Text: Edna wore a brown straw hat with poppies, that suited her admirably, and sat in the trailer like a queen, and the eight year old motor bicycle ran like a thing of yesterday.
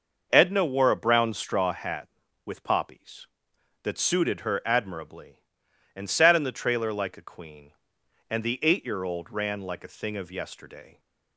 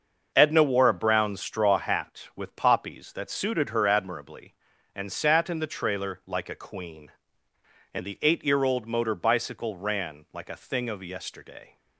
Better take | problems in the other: second | starts louder than the rest; noticeable; until 1.3 s; 6 dB; also in the second // skips "motor bicycle"; at 9.3 s

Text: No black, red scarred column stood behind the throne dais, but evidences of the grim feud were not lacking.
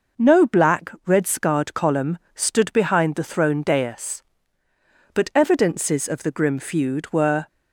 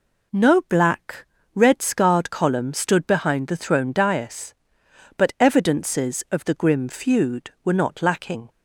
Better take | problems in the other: second | pauses between "column" and "stood"; slight; at 2.1 s; 0.16 s long // stops before "not lacking"; at 7.4 s

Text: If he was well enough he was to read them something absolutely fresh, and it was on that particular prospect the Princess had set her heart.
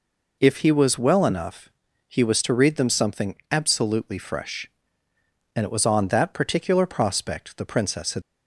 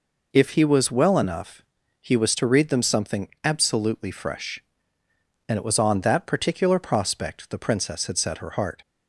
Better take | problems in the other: second | pauses between "enough" and "he"; at 1.6 s; 0.40 s long; also in the second // pauses between "something" and "absolutely"; slight; at 3.3 s; 0.16 s long; slight in the second // stops before "set her heart"; at 8.2 s

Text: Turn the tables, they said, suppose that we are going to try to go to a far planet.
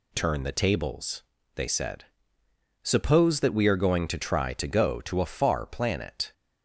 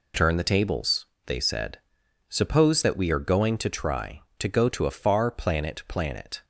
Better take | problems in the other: first | says "planet" twice; at 5.8 s

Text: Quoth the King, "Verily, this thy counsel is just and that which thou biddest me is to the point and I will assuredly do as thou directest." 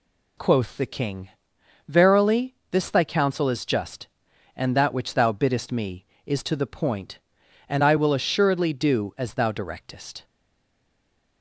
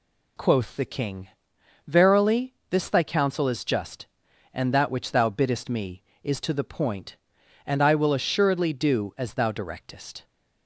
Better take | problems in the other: second | stays silent after the last word; noticeable; from 10.2 s on; 1.2 s long

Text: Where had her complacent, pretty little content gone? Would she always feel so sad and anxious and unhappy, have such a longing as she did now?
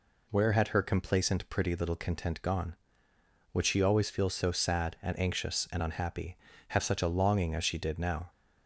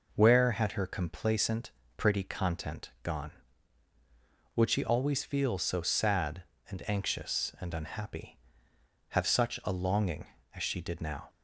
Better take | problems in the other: first | skips "little"; at 2.2 s

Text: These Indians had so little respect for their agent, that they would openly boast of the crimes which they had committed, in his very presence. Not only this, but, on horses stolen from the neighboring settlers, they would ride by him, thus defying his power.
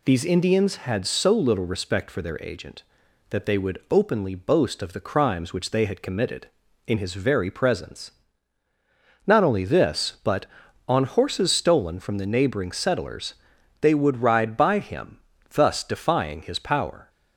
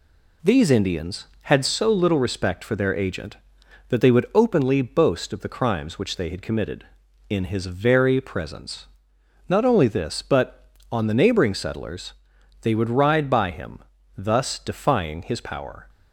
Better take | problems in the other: first | skips "horses stolen from"; at 11.0 s

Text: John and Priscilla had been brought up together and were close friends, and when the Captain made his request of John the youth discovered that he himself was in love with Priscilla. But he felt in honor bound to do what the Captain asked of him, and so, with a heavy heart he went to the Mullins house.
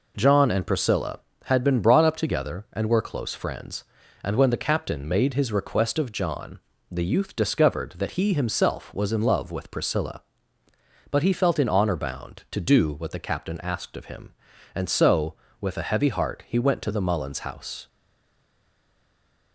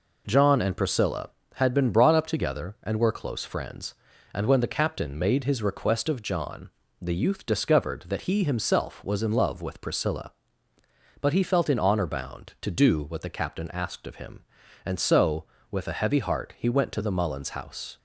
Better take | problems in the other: second | pauses between "John" and "the"; slight; at 6.5 s; 0.30 s long; slight in the second // stays silent after the last word; noticeable; from 17.8 s on; 1.7 s long

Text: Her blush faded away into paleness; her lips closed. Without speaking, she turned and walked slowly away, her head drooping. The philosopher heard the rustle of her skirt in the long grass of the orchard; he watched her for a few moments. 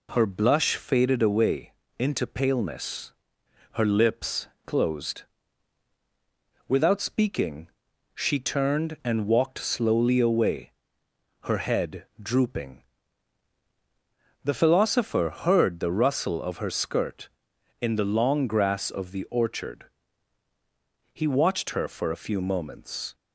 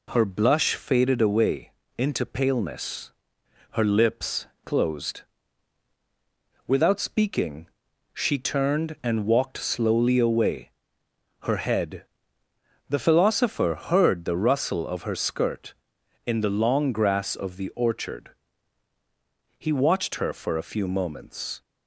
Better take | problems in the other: first | pauses between "away" and "into"; slight; at 1.6 s; 0.26 s long; slight in the first // pauses between "lips" and "closed"; slight; at 4.4 s; 0.18 s long; slight in the first // skips "drooping"; at 12.4 s

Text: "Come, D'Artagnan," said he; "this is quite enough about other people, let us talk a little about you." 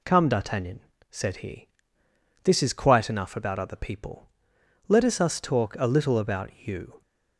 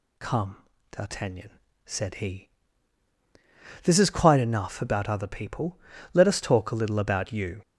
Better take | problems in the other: second | says "us" twice; at 5.2 s // pauses between "about" and "you"; slight; at 6.4 s; 0.16 s long

